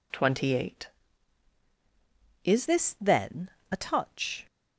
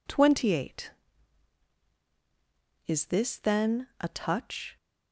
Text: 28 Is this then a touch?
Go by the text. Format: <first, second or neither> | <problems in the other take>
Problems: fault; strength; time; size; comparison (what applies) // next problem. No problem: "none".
second | changes voice at "this"; from 2.6 s on; 1.8 s long // pauses between "then" and "a"; slight; at 3.4 s; 0.22 s long